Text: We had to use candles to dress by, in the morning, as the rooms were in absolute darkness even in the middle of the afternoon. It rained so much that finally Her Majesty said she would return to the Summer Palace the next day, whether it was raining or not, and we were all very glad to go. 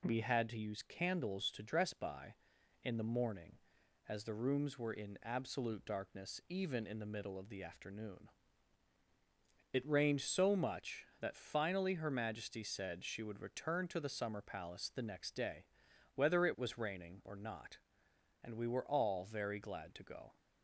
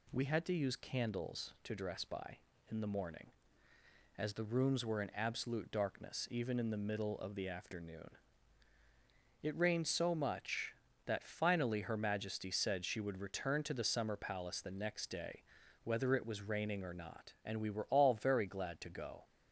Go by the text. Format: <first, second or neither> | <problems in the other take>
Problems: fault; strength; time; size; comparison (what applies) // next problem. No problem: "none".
neither | none